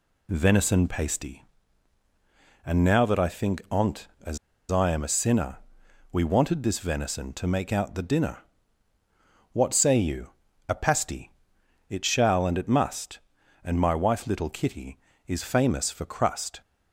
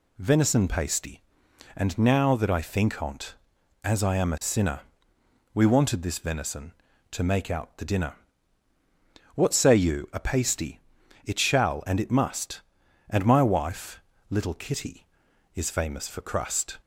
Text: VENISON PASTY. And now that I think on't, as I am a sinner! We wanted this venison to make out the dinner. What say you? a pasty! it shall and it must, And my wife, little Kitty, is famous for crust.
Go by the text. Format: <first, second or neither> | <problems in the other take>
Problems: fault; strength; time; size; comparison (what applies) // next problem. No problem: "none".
second | pauses between "as" and "I"; slight; at 4.3 s; 0.33 s long